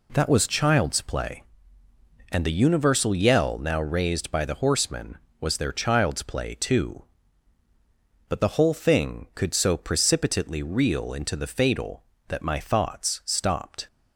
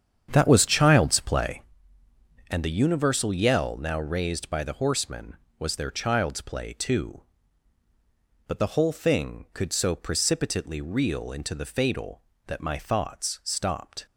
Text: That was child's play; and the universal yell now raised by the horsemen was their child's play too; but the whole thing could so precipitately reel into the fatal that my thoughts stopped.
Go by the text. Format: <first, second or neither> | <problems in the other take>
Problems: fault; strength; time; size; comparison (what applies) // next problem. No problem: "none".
first | starts louder than the rest; strong; until 1.8 s; 8 dB